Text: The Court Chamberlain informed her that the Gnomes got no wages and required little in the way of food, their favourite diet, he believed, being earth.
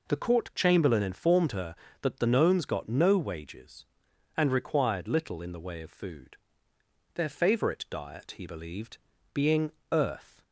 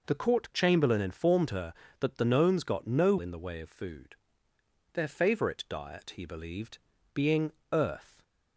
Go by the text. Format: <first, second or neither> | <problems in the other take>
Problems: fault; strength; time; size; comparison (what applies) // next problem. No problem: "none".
first | skips "wages and required little"; at 3.1 s // pauses between "being" and "earth"; slight; at 7.5 s; 0.20 s long; slight in the first